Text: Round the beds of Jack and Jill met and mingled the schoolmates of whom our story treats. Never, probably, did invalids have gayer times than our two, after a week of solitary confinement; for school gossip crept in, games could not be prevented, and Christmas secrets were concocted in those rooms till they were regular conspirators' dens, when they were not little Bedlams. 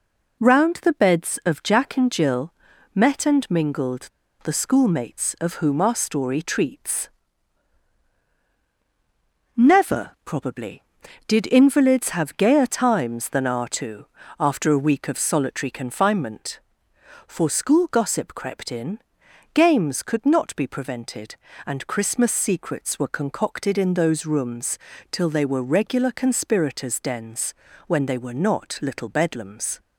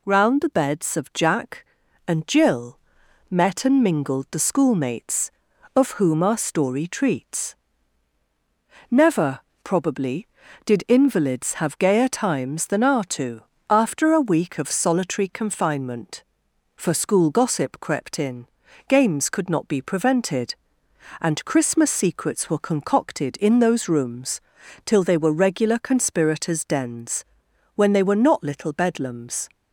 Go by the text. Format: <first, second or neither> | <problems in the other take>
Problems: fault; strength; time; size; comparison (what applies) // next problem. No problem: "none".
second | pauses between "Jill" and "met"; at 2.5 s; 0.40 s long; noticeable in the second // pauses between "mingled" and "the"; slight; at 4.0 s; 0.35 s long // pauses between "rooms" and "till"; slight; at 24.7 s; 0.34 s long; also in the second